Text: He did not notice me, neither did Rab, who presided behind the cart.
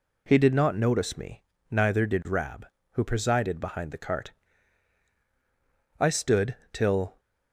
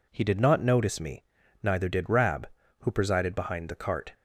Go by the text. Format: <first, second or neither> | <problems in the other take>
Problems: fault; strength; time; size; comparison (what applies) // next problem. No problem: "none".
second | goes on to say "I stood till"; noticeable; from 5.9 s on; 1.2 s long